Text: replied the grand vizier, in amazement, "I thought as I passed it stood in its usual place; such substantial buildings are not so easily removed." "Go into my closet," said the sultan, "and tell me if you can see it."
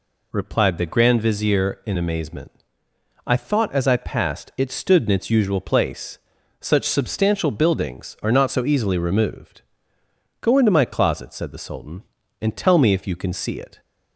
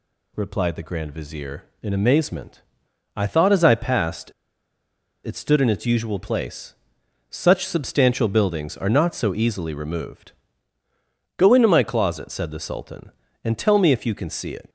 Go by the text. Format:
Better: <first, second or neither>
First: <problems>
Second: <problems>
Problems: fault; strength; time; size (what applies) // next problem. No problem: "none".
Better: first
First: none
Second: pauses between "passed" and "it"; noticeable; at 4.3 s; 0.93 s long